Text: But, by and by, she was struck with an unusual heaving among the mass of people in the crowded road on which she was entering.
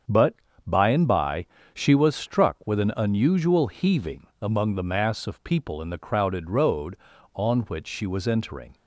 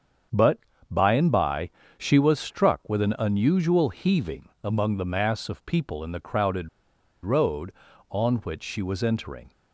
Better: first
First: starts louder than the rest; strong; until 1.3 s; 7 dB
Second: starts louder than the rest; strong; until 1.6 s; 7 dB // pauses between "crowded" and "road"; noticeable; at 6.6 s; 0.55 s long

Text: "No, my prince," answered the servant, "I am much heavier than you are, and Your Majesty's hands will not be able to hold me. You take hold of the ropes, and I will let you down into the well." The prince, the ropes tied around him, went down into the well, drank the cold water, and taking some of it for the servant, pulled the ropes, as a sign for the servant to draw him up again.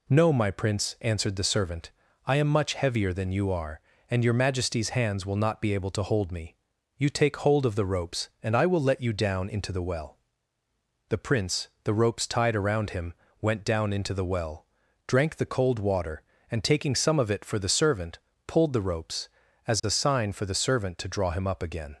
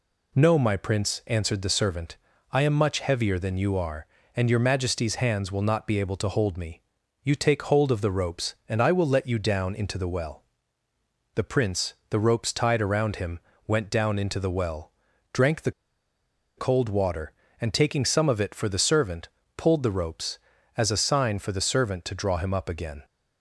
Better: first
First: none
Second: pauses between "the" and "cold"; noticeable; at 15.7 s; 0.86 s long

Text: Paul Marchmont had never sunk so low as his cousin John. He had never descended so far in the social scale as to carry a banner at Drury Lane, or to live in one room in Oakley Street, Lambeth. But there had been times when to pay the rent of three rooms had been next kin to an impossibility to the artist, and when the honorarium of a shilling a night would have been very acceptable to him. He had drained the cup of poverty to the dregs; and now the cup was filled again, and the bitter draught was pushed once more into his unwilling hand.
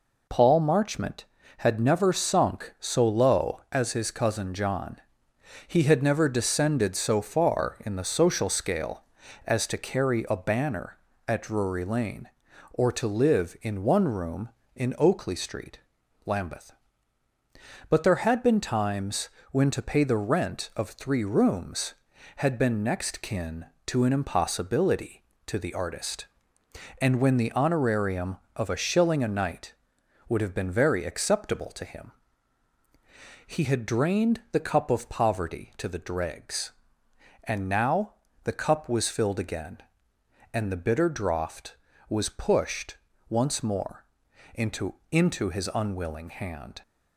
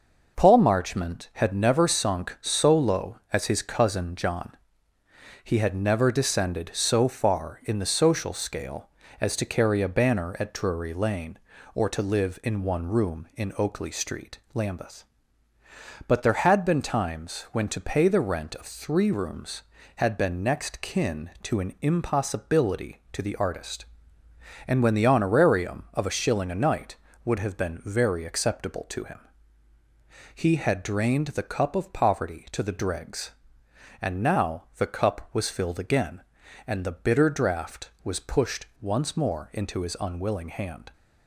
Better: second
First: pauses between "times" and "when"; slight; at 19.2 s; 0.24 s long // pauses between "now" and "the"; slight; at 38.1 s; 0.32 s long // pauses between "pushed" and "once"; slight; at 42.9 s; 0.34 s long // pauses between "more" and "into"; noticeable; at 44.0 s; 0.52 s long // says "into" twice; at 45.1 s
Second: none

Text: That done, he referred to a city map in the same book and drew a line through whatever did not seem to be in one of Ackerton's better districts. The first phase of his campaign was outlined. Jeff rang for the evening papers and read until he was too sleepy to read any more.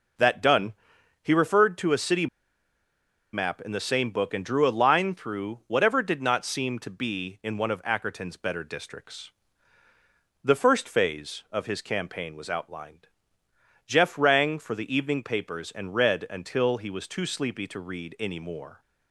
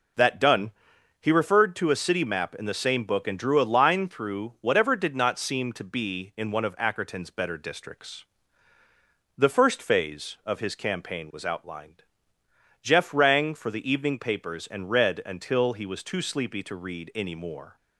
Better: second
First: pauses between "city" and "map"; at 2.2 s; 1.0 s long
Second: none

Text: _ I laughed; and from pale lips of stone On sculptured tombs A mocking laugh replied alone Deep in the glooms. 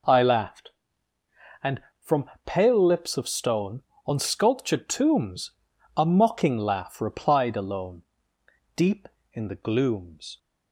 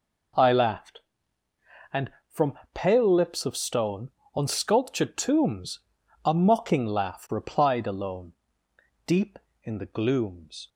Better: neither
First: pauses between "from" and "pale"; slight; at 2.2 s; 0.16 s long // pauses between "tombs" and "A"; noticeable; at 5.4 s; 0.46 s long // pauses between "alone" and "Deep"; noticeable; at 8.0 s; 0.72 s long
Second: pauses between "from" and "pale"; slight; at 2.5 s; 0.16 s long // pauses between "tombs" and "A"; noticeable; at 5.7 s; 0.46 s long // pauses between "alone" and "Deep"; noticeable; at 8.3 s; 0.72 s long

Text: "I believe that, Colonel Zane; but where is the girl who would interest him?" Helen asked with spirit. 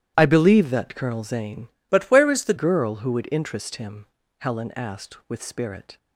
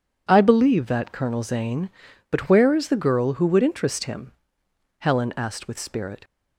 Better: second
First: starts louder than the rest; strong; until 1.1 s; 12.5 dB // changes voice from "but" to "the"; from 1.9 to 2.5 s; 0.6 s long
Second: none

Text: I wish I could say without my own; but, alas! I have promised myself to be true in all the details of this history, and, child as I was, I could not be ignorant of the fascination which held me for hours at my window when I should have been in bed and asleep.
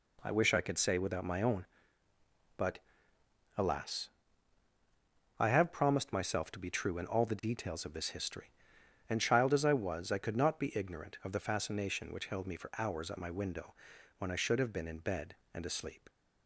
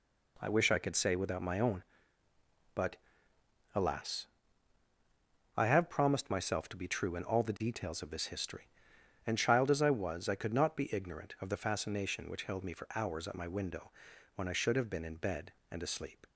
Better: neither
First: pauses between "window" and "when"; at 13.7 s; 0.44 s long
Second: pauses between "window" and "when"; at 13.9 s; 0.44 s long

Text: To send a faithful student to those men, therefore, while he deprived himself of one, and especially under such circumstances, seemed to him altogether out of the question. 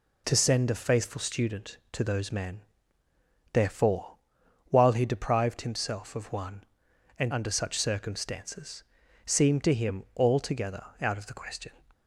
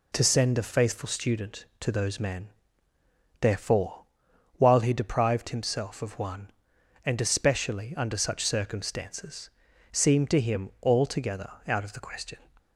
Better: second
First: skips "especially"; at 7.3 s // pauses between "altogether" and "out"; slight; at 10.8 s; 0.16 s long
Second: pauses between "altogether" and "out"; slight; at 11.4 s; 0.16 s long

